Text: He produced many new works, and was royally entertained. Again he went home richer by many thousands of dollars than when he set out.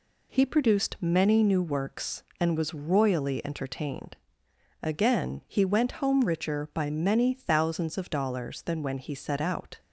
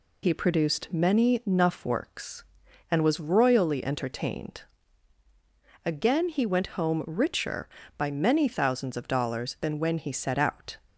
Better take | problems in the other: first | says "nuff" for "new"; at 1.4 s

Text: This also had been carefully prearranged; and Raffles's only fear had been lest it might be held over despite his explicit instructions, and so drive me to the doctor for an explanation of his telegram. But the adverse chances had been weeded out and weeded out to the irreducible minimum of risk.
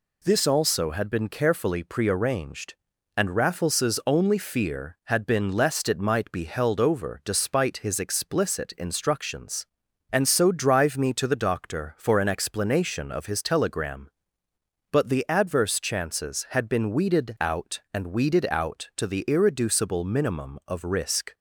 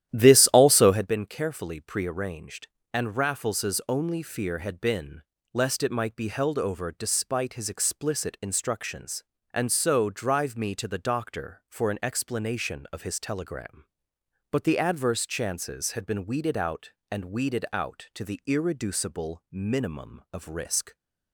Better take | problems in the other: first | starts louder than the rest; strong; until 1.1 s; 11.5 dB // pauses between "been" and "lest"; slight; at 5.2 s; 0.30 s long

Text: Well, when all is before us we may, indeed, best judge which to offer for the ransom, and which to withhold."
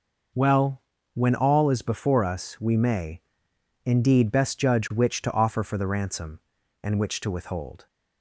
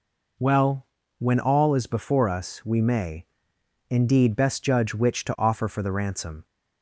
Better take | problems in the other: first | stops before "and which to withhold"; at 6.4 s

